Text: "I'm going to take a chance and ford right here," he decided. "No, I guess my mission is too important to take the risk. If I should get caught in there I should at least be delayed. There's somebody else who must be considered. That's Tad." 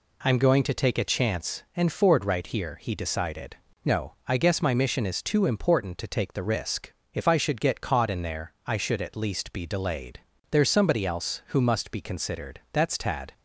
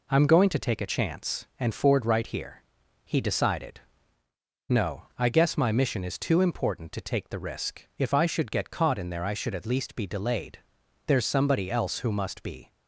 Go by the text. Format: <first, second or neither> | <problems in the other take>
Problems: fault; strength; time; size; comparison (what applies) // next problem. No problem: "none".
first | stops before "considered That's Tad"; at 12.7 s